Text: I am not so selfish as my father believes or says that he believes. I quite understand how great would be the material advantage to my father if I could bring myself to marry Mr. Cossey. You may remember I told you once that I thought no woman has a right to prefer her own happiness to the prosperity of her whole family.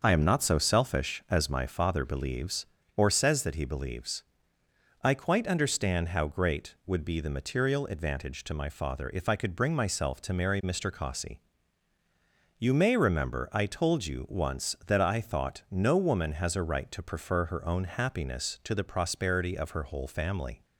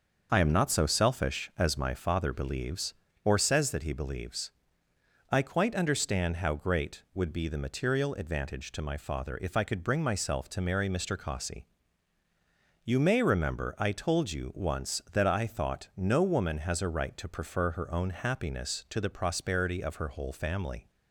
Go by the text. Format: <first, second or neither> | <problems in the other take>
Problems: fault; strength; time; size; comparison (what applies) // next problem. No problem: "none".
neither | none